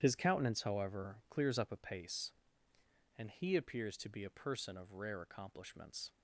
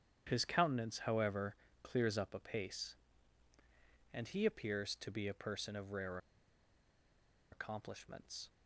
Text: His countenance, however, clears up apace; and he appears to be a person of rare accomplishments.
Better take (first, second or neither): first